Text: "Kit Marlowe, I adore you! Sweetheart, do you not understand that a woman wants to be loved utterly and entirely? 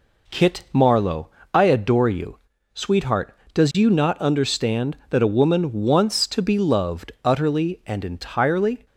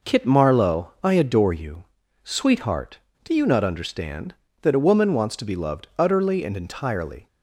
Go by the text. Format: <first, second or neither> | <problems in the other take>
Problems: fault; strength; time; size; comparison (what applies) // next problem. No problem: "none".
second | says "does" for "do"; at 3.5 s